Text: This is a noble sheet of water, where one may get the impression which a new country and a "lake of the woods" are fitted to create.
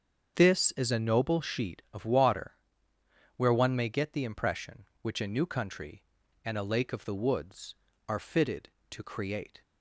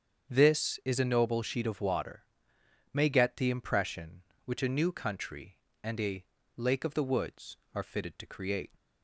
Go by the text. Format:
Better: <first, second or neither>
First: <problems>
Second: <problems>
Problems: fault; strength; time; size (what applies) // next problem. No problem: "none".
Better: first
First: starts louder than the rest; strong; until 1.3 s; 7 dB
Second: starts louder than the rest; strong; until 1.3 s; 7 dB // skips "where one"; at 2.5 s // pauses between "a" and "lake"; slight; at 6.2 s; 0.32 s long